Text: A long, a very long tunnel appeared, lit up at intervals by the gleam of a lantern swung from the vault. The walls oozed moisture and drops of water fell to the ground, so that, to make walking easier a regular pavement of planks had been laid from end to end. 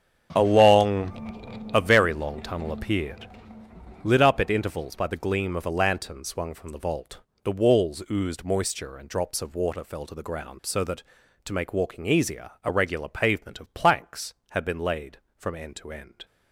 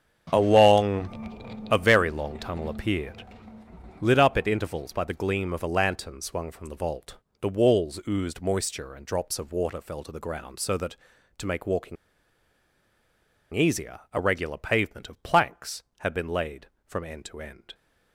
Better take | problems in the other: first | starts louder than the rest; strong; until 1.3 s; 7.5 dB; strong in the first // pauses between "walking" and "easier"; strong; at 11.9 s; 1.5 s long

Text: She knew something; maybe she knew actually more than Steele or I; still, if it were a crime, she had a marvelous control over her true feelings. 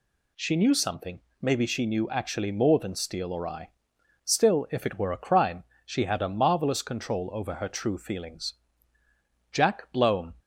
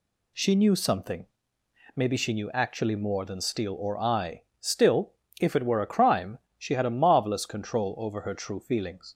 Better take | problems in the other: second | goes on to say "Jack Blome"; noticeable; from 9.5 s on; 0.80 s long

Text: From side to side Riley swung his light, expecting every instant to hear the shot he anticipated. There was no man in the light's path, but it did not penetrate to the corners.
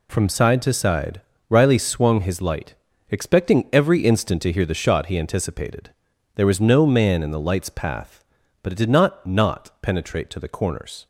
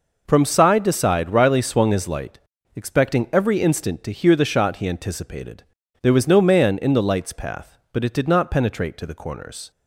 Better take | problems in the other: second | pauses between "side" and "Riley"; slight; at 1.2 s; 0.28 s long // says "not" twice; at 9.2 s

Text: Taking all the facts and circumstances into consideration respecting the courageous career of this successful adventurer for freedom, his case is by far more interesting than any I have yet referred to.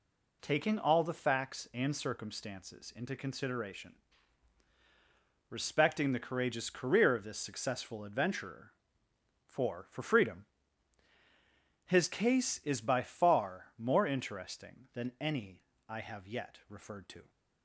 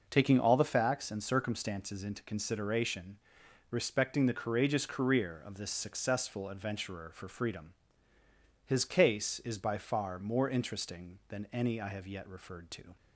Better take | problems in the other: second | pauses between "consideration" and "respecting"; strong; at 3.9 s; 1.5 s long; noticeable in the second // says "for" twice; at 9.8 s // pauses between "any" and "I"; slight; at 15.6 s; 0.24 s long

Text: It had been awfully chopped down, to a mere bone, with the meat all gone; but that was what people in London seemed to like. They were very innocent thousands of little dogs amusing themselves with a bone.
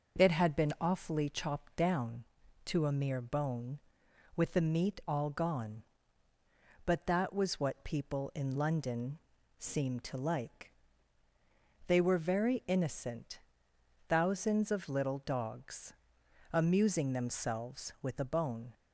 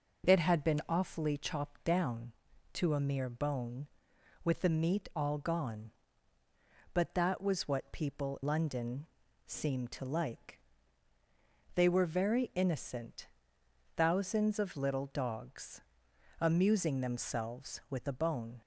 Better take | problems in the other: first | skips "in"; at 8.4 s // pauses between "London" and "seemed"; at 9.0 s; 0.42 s long; also in the first // pauses between "innocent" and "thousands"; noticeable; at 13.2 s; 0.68 s long; noticeable in the first // pauses between "dogs" and "amusing"; noticeable; at 15.7 s; 0.62 s long; noticeable in the first

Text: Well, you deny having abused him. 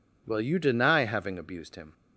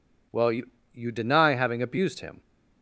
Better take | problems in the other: first | says "you" twice; at 0.9 s

